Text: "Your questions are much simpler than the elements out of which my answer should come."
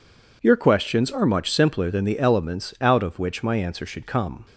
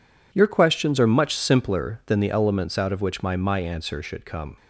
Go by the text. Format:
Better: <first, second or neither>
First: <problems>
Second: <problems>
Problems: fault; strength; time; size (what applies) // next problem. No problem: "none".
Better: first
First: none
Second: says "my" twice; at 3.3 s